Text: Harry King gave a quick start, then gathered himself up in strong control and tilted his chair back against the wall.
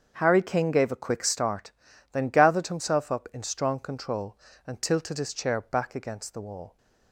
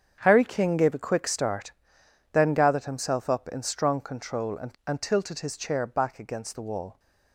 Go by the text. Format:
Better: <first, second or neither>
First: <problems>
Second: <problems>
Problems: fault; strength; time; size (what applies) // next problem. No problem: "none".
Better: first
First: starts louder than the rest; until 1.1 s; 7 dB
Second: starts louder than the rest; strong; until 1.2 s; 8 dB // says "and" twice; at 4.8 s